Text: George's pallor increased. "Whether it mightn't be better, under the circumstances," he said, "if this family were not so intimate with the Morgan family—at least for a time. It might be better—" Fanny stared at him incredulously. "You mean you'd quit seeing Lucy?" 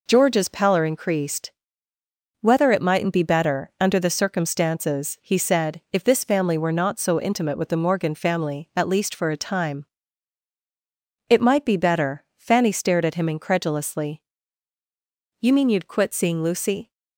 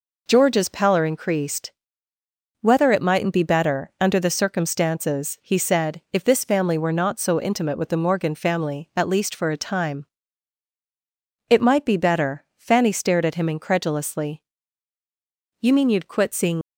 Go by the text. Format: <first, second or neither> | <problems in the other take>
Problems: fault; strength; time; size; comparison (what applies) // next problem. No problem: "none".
first | stops before "Lucy"; at 16.6 s